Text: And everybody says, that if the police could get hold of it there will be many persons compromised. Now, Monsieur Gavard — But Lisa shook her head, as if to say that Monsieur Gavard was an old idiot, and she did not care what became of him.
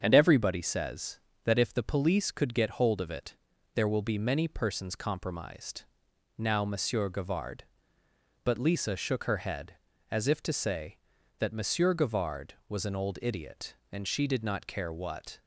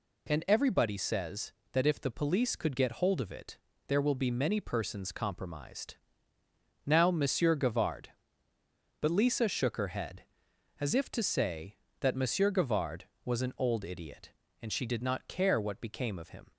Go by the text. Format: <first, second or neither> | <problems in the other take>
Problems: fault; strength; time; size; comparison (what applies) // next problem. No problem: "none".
second | starts louder than the rest; strong; until 1.0 s; 7 dB // pauses between "it" and "there"; at 3.3 s; 0.40 s long; slight in the second // stops before "became of him"; at 15.4 s